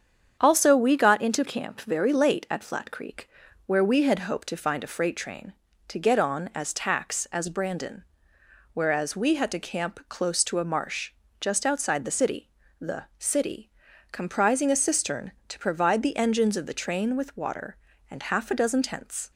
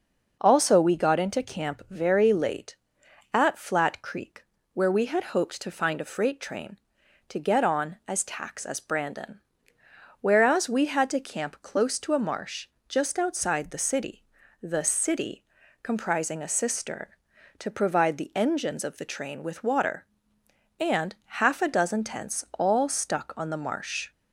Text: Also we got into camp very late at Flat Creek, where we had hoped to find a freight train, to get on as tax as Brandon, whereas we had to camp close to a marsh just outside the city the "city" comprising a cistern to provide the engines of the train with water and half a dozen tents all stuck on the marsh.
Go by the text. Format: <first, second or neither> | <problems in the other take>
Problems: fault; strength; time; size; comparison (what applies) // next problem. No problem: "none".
second | starts louder than the rest; strong; until 1.4 s; 8 dB // pauses between "marsh" and "just"; slight; at 11.1 s; 0.28 s long; slight in the second // pauses between "city" and "the"; slight; at 12.4 s; 0.32 s long; also in the second // pauses between "city" and "comprising"; at 13.7 s; 0.40 s long; also in the second // stops before "all stuck on the marsh"; at 19.3 s